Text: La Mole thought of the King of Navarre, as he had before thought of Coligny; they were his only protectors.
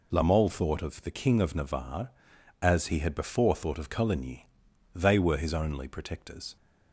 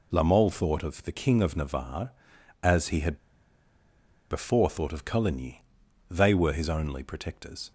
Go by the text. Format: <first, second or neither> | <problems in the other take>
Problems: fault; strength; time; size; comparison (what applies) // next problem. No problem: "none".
first | pauses between "had" and "before"; at 3.1 s; 1.1 s long